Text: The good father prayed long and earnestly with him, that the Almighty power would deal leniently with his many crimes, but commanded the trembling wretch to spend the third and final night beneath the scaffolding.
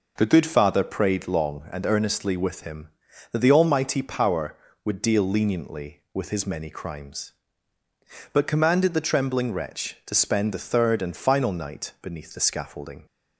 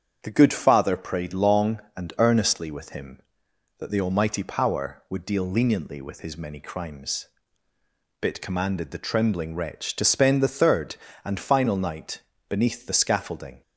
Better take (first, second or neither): first